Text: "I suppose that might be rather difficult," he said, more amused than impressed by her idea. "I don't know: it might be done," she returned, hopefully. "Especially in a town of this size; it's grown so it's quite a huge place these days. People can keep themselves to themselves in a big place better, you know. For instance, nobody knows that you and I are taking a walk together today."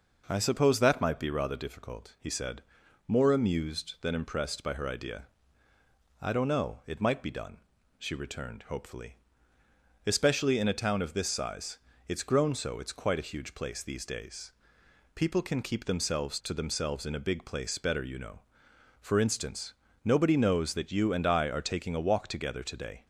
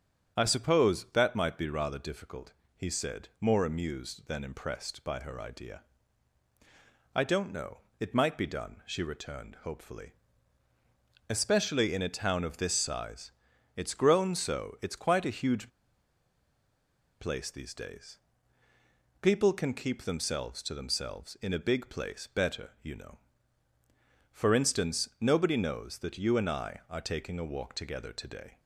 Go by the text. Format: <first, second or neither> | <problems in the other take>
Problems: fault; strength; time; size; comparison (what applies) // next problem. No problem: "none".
first | starts louder than the rest; strong; until 1.4 s; 7.5 dB // pauses between "huge" and "place"; strong; at 15.6 s; 1.5 s long